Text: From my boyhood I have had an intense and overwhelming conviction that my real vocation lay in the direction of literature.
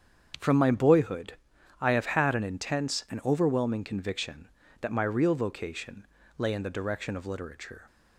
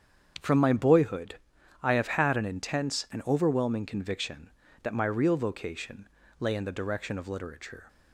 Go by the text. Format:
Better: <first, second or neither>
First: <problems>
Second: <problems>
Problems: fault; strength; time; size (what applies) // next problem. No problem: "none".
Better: neither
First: starts louder than the rest; strong; until 1.8 s; 8 dB // pauses between "boyhood" and "I"; noticeable; at 1.3 s; 0.48 s long // pauses between "vocation" and "lay"; slight; at 6.0 s; 0.32 s long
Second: starts louder than the rest; strong; until 1.8 s; 7.5 dB // pauses between "boyhood" and "I"; noticeable; at 1.3 s; 0.48 s long // pauses between "vocation" and "lay"; slight; at 6.0 s; 0.32 s long